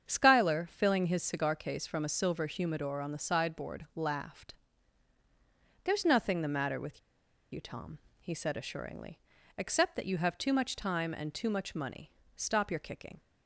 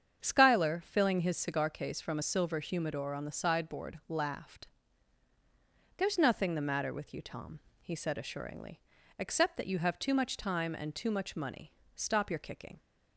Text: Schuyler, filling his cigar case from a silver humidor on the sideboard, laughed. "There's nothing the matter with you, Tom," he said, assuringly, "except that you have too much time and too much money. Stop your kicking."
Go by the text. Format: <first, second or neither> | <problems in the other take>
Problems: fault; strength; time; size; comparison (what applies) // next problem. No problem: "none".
second | starts louder than the rest; strong; until 1.1 s; 8 dB; strong in the second // pauses between "with" and "you"; noticeable; at 6.9 s; 0.52 s long